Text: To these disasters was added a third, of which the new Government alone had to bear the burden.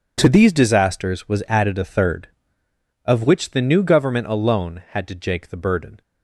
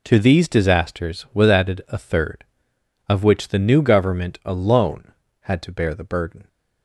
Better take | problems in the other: second | says "jake" for "bear"; at 5.1 s

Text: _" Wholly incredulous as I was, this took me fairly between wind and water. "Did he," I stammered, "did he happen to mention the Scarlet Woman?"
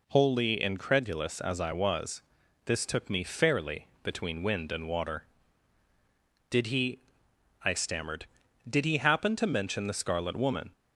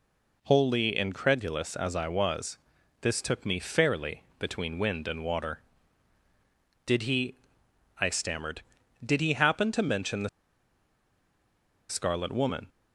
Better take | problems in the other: first | pauses between "fairly" and "between"; slight; at 4.2 s; 0.16 s long; slight in the first // pauses between "the" and "Scarlet"; strong; at 10.2 s; 1.6 s long

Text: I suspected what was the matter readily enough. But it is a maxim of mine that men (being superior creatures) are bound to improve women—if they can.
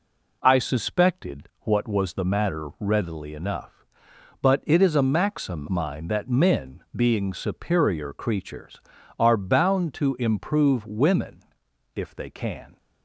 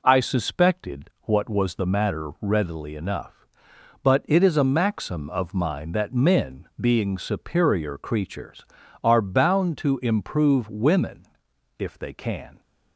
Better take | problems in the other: second | skips "of"; at 5.6 s

